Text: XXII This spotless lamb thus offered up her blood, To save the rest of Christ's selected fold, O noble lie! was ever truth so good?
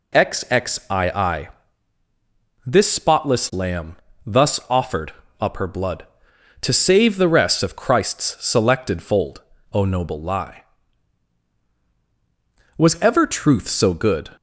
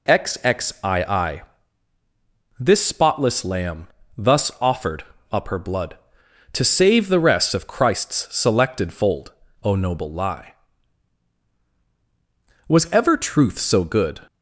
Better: neither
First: pauses between "XXII" and "This"; at 1.4 s; 1.1 s long // pauses between "lamb" and "thus"; slight; at 3.9 s; 0.28 s long // pauses between "offered" and "up"; slight; at 5.1 s; 0.30 s long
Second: pauses between "XXII" and "This"; at 1.4 s; 1.1 s long // pauses between "lamb" and "thus"; slight; at 3.8 s; 0.28 s long // pauses between "offered" and "up"; slight; at 5.0 s; 0.30 s long

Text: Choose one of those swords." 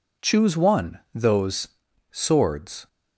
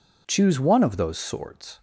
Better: second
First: skips "of"; at 1.0 s // pauses between "those" and "swords"; at 1.6 s; 0.42 s long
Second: none

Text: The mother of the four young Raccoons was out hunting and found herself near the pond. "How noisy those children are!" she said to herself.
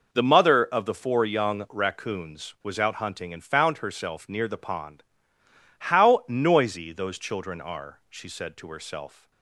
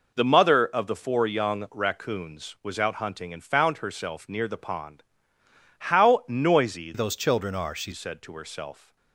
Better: first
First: none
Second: changes voice from "those" to "she"; from 6.9 to 7.9 s; 1.0 s long

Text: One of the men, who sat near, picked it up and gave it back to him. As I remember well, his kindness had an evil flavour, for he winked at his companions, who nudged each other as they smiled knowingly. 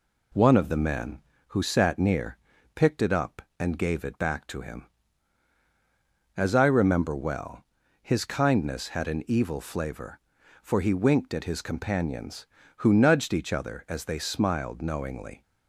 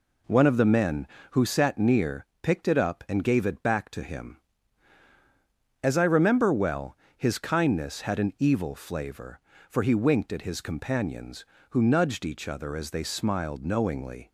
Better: neither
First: none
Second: none

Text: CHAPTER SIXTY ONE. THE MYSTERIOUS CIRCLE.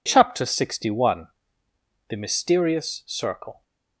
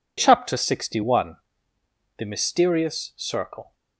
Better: neither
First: none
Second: none

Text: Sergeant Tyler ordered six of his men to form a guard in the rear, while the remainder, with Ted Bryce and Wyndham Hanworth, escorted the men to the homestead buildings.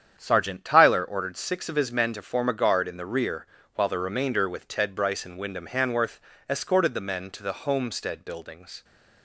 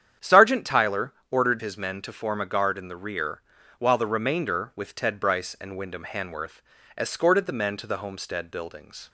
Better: first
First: starts louder than the rest; strong; until 1.1 s; 8.5 dB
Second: starts louder than the rest; strong; until 1.3 s; 9 dB // pauses between "Tyler" and "ordered"; slight; at 1.1 s; 0.16 s long // skips "six of"; at 1.6 s

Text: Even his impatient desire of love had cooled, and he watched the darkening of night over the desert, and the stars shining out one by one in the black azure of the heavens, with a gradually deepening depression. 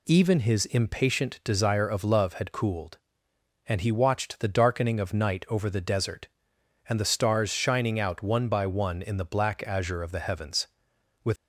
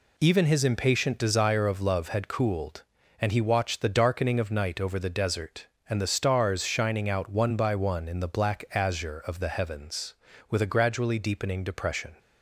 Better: second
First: stops before "a gradually deepening depression"; at 11.3 s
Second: none

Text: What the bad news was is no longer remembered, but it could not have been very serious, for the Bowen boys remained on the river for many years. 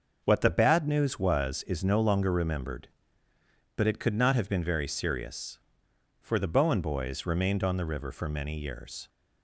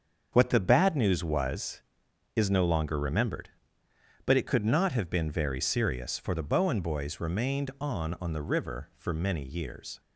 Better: first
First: starts louder than the rest; noticeable; until 1.2 s; 6 dB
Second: starts louder than the rest; until 1.3 s; 7 dB // says "on" twice; at 8.1 s

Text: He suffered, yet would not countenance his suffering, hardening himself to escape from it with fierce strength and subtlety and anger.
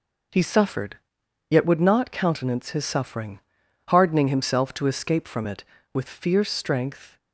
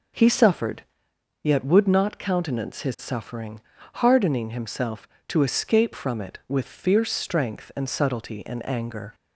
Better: second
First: stops before "and subtlety and anger"; at 7.1 s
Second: none

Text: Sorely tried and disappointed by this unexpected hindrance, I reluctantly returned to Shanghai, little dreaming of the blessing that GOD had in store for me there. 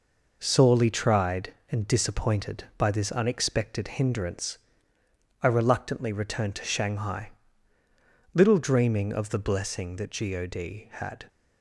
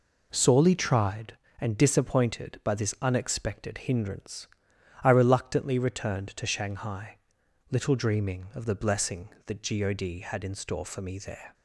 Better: second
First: stops before "in store for me there"; at 11.2 s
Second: none

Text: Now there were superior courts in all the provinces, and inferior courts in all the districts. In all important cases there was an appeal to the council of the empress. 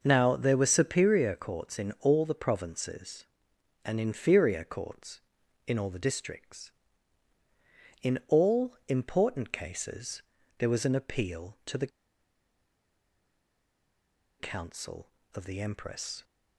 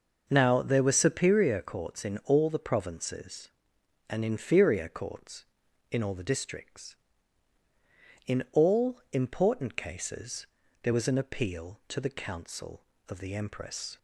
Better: second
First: pauses between "cases" and "there"; slight; at 10.2 s; 0.34 s long // pauses between "the" and "council"; strong; at 11.9 s; 2.5 s long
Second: pauses between "cases" and "there"; slight; at 10.4 s; 0.34 s long

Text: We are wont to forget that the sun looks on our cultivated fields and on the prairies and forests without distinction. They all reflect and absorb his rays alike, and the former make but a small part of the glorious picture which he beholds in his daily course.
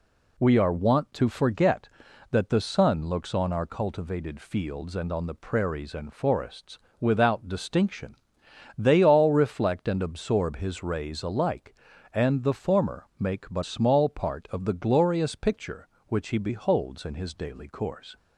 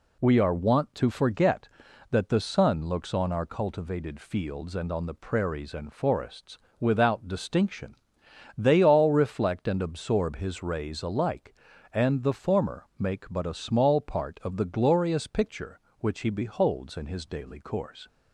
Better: second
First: pauses between "forests" and "without"; slight; at 6.7 s; 0.22 s long // skips "a"; at 13.6 s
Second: pauses between "forests" and "without"; slight; at 6.5 s; 0.22 s long

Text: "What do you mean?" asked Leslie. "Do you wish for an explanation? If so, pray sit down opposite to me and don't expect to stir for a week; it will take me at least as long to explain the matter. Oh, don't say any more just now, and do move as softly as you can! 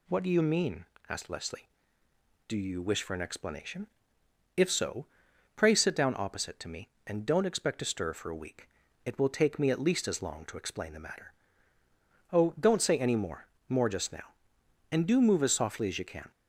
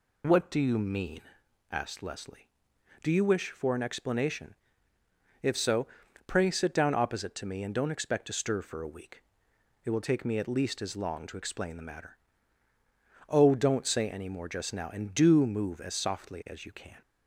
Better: second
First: says "more" twice; at 13.6 s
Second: none

